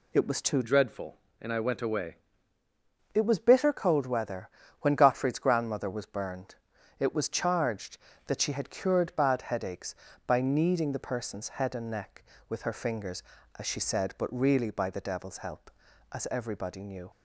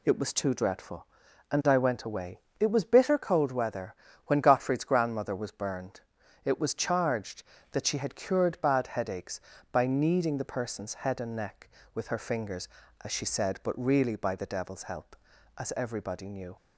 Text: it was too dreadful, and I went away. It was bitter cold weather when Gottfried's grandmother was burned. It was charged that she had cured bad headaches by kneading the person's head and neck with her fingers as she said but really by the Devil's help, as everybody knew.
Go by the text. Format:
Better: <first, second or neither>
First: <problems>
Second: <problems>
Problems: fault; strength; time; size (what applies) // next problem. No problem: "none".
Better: second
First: changes voice from "dreadful" to "away"; from 0.6 to 2.1 s; 1.5 s long // pauses between "weather" and "when"; slight; at 4.4 s; 0.32 s long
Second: pauses between "weather" and "when"; slight; at 3.9 s; 0.32 s long